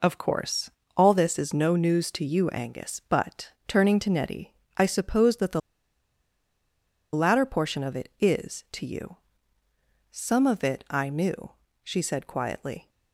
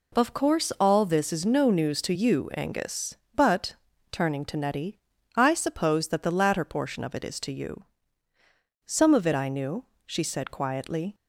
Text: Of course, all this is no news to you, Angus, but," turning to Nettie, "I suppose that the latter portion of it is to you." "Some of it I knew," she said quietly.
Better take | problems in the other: second | pauses between "the" and "latter"; strong; at 5.6 s; 1.5 s long

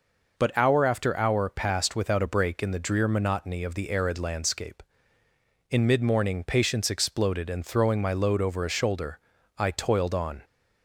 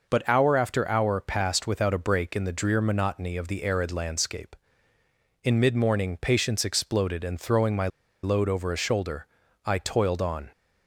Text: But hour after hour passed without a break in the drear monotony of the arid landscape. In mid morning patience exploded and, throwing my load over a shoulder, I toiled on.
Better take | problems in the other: first | pauses between "my" and "load"; slight; at 7.8 s; 0.35 s long

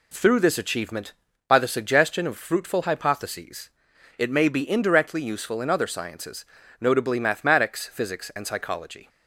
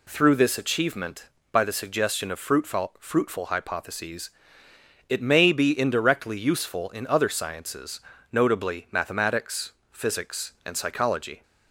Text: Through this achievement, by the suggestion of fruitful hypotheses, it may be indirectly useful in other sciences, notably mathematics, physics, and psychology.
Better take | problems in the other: first | says "fruitful" twice; at 2.9 s

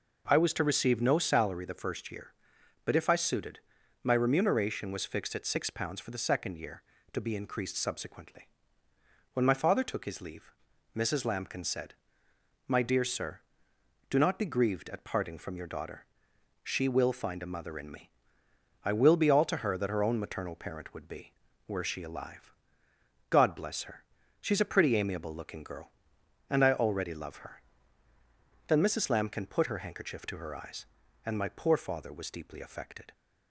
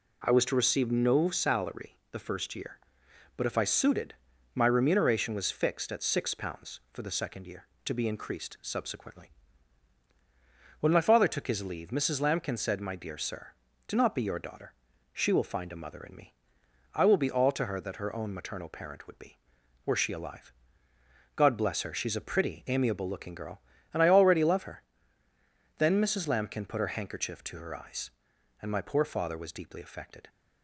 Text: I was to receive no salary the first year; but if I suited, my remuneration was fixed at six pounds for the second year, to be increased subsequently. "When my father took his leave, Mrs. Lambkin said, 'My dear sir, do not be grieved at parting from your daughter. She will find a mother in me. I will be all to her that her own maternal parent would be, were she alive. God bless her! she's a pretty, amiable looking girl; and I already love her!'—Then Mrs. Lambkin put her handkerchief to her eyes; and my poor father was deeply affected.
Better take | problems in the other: first | pauses between "salary" and "the"; slight; at 1.9 s; 0.16 s long // skips "grieved at parting from"; at 14.2 s

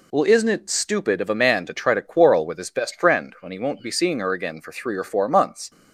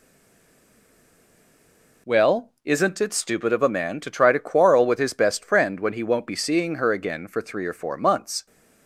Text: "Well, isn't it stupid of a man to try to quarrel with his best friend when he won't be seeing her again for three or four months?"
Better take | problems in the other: first | stays silent before the first word; noticeable; until 2.0 s; 2.0 s long

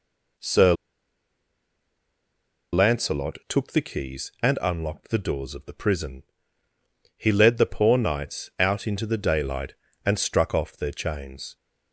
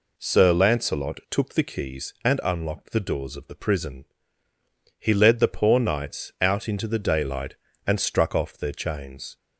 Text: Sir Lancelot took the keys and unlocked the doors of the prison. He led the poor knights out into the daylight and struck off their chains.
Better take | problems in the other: second | pauses between "Sir" and "Lancelot"; strong; at 0.7 s; 1.9 s long

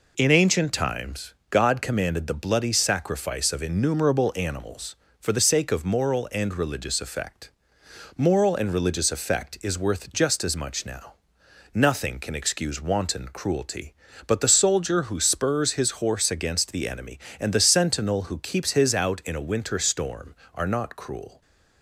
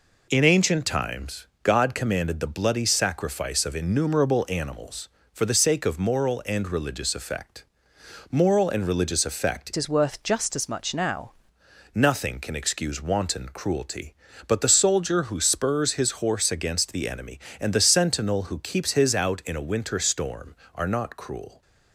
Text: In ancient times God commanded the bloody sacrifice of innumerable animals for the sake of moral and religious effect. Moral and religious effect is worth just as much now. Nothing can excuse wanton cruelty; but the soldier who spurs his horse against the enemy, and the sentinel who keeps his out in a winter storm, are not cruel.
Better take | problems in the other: first | pauses between "times" and "God"; slight; at 1.4 s; 0.18 s long; slight in the first // changes voice from "is" to "now"; from 9.7 to 11.3 s; 1.6 s long

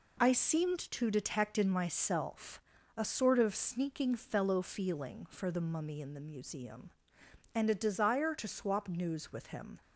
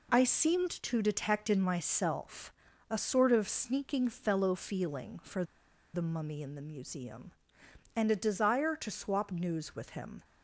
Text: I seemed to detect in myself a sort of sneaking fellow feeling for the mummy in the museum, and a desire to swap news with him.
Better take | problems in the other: first | pauses between "myself" and "a"; at 2.5 s; 0.38 s long; also in the first // pauses between "for" and "the"; noticeable; at 5.4 s; 0.50 s long

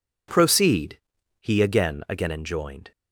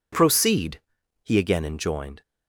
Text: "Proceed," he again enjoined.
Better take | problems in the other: second | says "again" twice; at 2.0 s

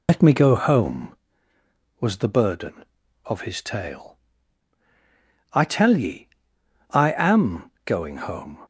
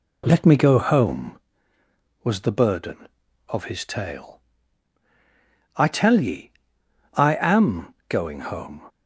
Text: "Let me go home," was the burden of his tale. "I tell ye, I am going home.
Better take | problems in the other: second | loses the start of "Let"; at 0.0 s; 90 ms // pauses between "am" and "going"; slight; at 7.6 s; 0.16 s long; slight in the second

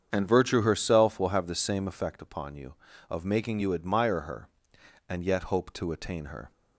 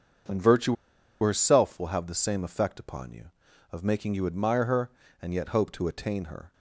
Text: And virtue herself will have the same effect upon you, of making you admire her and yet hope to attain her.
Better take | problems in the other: first | starts louder than the rest; until 1.7 s; 7 dB; strong in the first // pauses between "virtue" and "herself"; noticeable; at 0.7 s; 0.47 s long

